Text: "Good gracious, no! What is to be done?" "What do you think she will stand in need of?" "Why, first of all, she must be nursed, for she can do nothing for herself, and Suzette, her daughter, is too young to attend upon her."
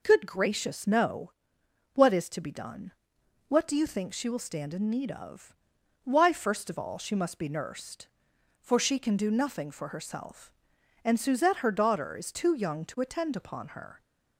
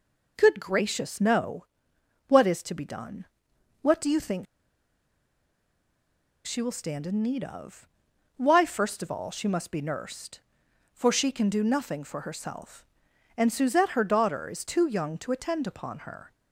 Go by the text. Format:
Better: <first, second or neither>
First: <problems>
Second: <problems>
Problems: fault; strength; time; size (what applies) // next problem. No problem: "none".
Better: first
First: none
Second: pauses between "think" and "she"; strong; at 4.4 s; 1.9 s long